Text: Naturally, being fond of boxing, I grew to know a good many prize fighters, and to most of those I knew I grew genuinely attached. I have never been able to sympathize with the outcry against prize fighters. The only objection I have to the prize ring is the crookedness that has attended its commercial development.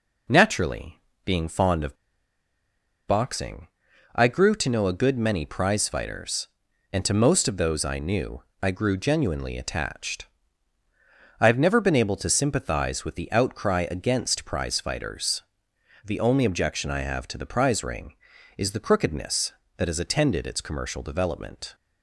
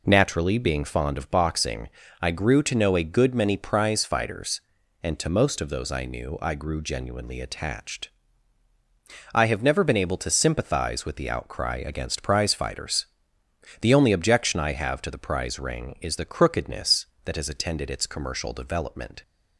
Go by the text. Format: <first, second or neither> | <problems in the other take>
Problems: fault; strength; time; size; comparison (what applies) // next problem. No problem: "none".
second | pauses between "of" and "boxing"; at 1.9 s; 1.1 s long // pauses between "knew" and "I"; slight; at 8.4 s; 0.20 s long